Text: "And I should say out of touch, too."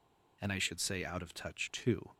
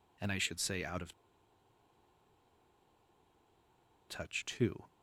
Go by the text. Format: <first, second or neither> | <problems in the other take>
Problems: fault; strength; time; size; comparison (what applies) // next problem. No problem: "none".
first | pauses between "of" and "touch"; strong; at 1.1 s; 2.9 s long